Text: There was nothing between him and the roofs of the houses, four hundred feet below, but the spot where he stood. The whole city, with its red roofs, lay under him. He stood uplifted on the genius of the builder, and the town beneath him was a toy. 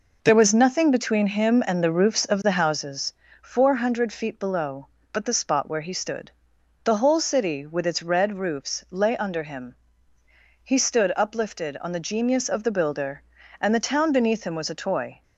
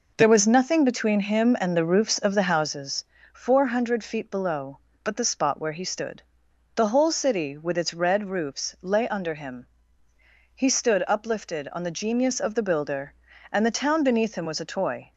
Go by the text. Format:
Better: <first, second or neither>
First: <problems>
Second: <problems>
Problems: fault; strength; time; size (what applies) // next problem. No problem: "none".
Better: neither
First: none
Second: none